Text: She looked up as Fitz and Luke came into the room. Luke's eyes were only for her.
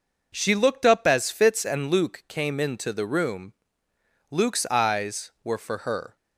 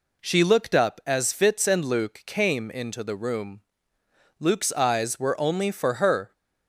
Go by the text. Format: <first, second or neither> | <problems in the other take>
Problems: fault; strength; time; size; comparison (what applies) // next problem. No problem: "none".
second | skips "only"; at 5.5 s